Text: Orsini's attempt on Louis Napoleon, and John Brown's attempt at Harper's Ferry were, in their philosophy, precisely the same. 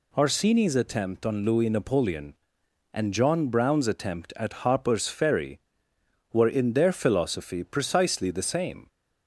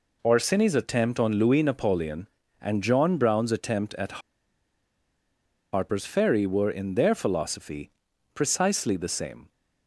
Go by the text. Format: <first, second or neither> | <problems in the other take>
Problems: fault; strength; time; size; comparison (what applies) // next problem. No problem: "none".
first | pauses between "at" and "Harper's"; strong; at 4.1 s; 1.5 s long